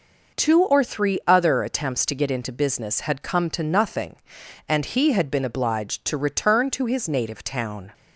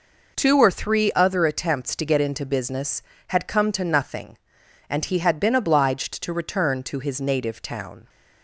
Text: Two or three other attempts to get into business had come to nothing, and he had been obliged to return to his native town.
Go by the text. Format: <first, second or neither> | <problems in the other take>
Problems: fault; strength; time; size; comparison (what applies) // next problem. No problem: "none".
neither | none